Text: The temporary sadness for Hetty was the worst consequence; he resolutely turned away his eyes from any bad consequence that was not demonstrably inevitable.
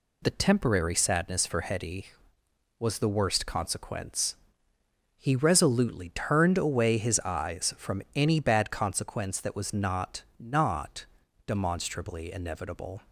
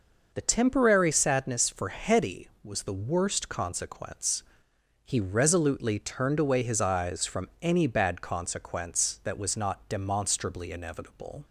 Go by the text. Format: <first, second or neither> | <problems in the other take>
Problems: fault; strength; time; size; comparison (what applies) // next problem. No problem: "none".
second | says "not" twice; at 10.3 s